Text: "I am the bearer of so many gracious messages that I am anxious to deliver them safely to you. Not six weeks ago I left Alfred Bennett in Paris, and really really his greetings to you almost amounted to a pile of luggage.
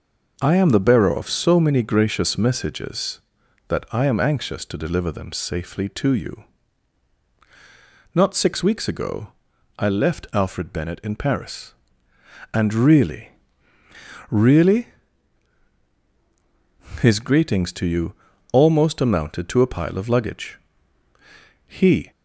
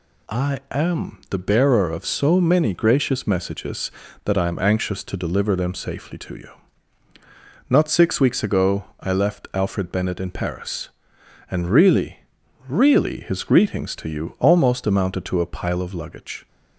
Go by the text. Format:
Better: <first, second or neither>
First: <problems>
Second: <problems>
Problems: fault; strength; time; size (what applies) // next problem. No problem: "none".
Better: second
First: pauses between "ago" and "I"; noticeable; at 9.2 s; 0.50 s long // pauses between "really" and "really"; noticeable; at 13.3 s; 0.98 s long // pauses between "really" and "his"; strong; at 14.8 s; 2.1 s long // pauses between "you" and "almost"; at 18.1 s; 0.40 s long // goes on to say "He"; slight; from 21.6 s on; 0.46 s long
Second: pauses between "ago" and "I"; slight; at 8.8 s; 0.16 s long // pauses between "really" and "really"; noticeable; at 12.1 s; 0.50 s long